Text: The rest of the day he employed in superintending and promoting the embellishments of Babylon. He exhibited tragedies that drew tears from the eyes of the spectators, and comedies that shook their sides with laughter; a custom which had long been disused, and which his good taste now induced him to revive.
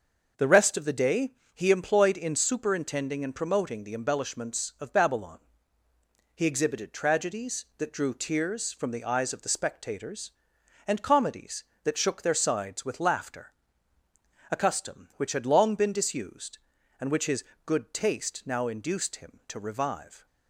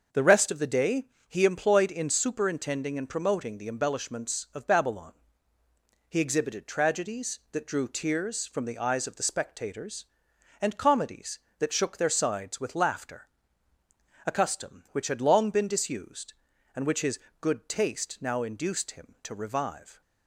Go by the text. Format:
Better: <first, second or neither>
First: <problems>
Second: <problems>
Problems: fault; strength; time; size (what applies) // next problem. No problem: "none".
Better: neither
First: starts louder than the rest; until 1.6 s; 6.5 dB // pauses between "day" and "he"; slight; at 1.3 s; 0.22 s long // pauses between "his" and "good"; slight; at 17.4 s; 0.20 s long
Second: starts louder than the rest; until 1.3 s; 6.5 dB // pauses between "day" and "he"; slight; at 1.0 s; 0.22 s long // pauses between "his" and "good"; slight; at 17.1 s; 0.20 s long